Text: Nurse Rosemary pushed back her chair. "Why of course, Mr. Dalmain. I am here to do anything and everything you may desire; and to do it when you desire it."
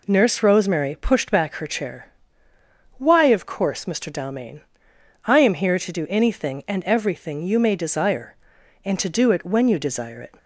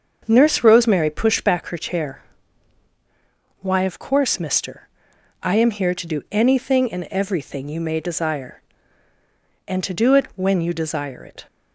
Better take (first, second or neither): first